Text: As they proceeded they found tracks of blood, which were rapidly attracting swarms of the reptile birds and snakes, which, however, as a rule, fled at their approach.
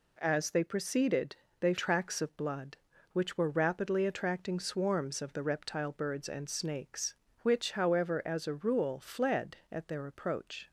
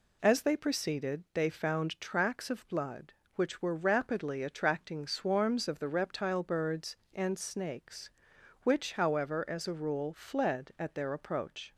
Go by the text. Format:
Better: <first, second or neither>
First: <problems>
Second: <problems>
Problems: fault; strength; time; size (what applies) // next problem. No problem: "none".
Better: second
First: pauses between "proceeded" and "they"; slight; at 1.3 s; 0.24 s long // skips "found"; at 1.7 s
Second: none